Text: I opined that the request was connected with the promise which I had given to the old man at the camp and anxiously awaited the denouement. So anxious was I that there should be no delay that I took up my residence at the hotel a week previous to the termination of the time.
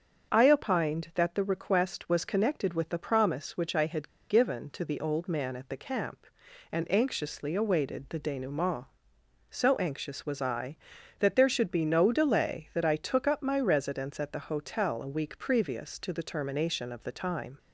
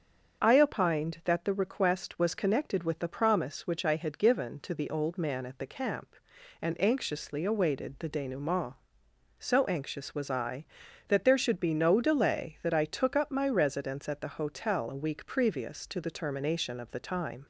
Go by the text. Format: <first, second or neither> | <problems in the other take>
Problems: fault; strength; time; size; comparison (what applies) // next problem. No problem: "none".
second | starts louder than the rest; until 1.3 s; 7 dB; also in the second // pauses between "had" and "given"; slight; at 4.0 s; 0.20 s long